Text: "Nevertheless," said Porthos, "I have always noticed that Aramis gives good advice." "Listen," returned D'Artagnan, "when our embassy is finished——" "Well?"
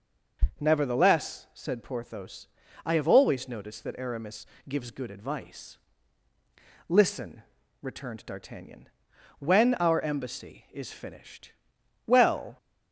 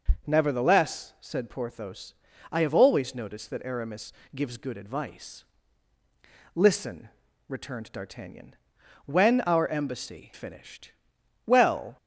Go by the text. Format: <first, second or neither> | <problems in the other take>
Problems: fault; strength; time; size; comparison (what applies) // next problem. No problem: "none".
first | pauses between "Aramis" and "gives"; slight; at 4.1 s; 0.24 s long; slight in the first // skips "is"; at 10.3 s